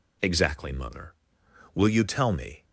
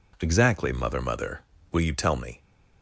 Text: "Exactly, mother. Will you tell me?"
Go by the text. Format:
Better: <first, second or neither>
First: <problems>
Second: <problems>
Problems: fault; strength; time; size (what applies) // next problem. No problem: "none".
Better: first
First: none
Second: says "mother" twice; at 1.0 s